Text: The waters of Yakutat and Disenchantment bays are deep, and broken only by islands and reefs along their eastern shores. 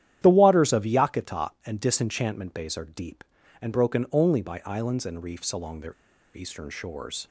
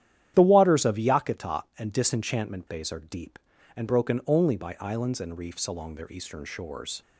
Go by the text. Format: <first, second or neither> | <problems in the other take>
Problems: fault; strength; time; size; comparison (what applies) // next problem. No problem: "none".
second | starts louder than the rest; strong; until 1.2 s; 10.5 dB; strong in the second // pauses between "their" and "eastern"; at 5.9 s; 0.42 s long